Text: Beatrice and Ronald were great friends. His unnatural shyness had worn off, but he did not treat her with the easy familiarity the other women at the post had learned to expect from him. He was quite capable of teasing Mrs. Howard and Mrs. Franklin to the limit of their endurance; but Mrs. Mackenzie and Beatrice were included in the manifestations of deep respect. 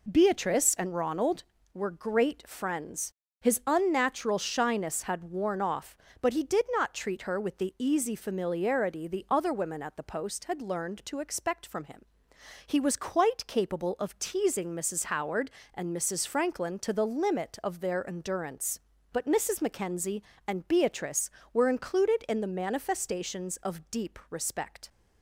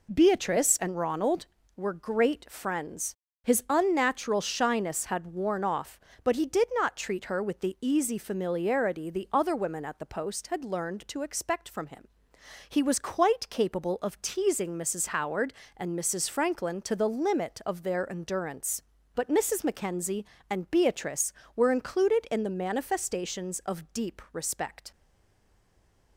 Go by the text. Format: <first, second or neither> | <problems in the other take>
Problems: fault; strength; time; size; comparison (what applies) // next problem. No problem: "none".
first | stays silent after the last word; noticeable; from 24.9 s on; 1.2 s long